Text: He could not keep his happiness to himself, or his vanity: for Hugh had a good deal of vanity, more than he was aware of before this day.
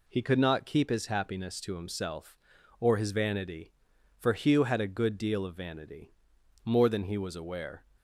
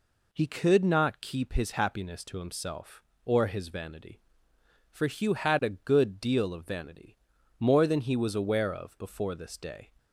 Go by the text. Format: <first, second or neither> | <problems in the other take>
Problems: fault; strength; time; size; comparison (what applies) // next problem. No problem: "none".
second | stops before "of before this day"; at 7.9 s